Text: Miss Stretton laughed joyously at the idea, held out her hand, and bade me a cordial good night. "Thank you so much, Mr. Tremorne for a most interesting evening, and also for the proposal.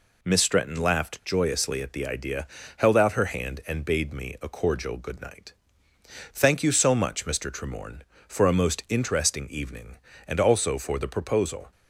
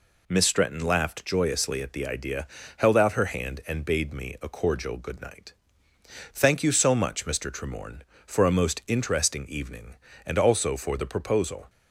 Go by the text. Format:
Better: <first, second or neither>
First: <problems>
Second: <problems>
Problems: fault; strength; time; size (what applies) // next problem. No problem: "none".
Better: neither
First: none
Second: none